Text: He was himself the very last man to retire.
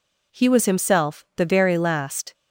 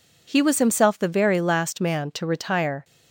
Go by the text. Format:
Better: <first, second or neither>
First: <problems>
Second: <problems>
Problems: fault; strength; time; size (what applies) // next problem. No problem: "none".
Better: second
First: stops before "man to retire"; at 2.3 s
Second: none